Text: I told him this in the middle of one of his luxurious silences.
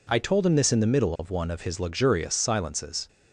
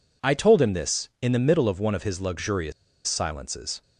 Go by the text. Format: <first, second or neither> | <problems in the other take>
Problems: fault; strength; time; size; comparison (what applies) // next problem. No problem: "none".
first | pauses between "luxurious" and "silences"; slight; at 2.7 s; 0.35 s long